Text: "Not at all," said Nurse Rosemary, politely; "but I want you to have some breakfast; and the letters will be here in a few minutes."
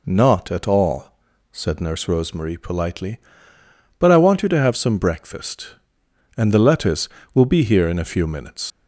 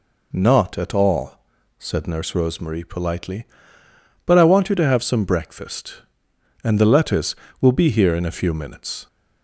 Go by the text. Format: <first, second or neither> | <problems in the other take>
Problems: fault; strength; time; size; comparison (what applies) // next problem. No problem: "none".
second | leaves "minutes" unfinished; at 8.7 s; 100 ms